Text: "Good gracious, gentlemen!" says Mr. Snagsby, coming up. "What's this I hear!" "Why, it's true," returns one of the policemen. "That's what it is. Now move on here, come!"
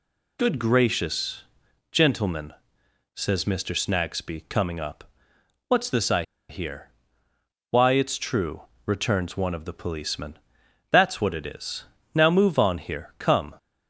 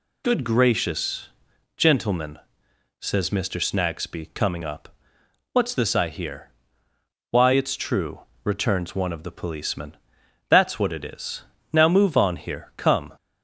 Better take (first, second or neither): second